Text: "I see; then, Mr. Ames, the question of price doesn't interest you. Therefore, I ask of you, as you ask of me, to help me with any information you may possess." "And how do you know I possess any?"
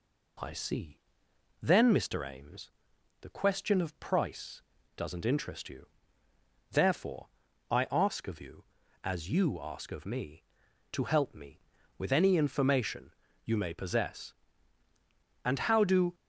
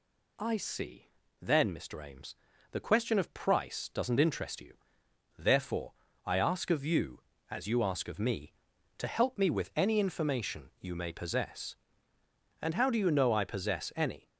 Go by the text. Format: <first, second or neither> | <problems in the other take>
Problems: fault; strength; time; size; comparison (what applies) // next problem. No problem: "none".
second | pauses between "price" and "doesn't"; slight; at 4.6 s; 0.32 s long // pauses between "information" and "you"; slight; at 13.1 s; 0.32 s long // stops before "you know I possess any"; at 16.1 s